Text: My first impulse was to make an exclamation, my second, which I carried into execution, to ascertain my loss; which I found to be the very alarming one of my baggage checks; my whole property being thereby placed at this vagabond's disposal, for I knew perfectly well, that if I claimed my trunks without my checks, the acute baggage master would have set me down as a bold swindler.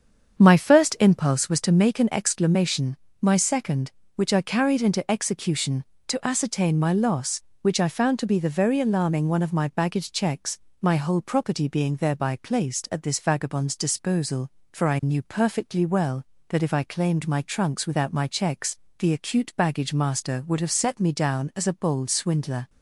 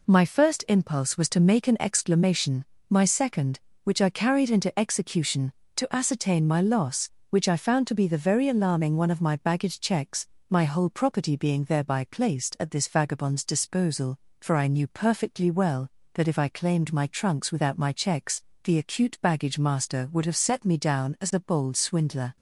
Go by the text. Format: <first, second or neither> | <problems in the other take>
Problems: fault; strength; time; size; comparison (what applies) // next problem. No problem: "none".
second | starts louder than the rest; strong; until 1.5 s; 7.5 dB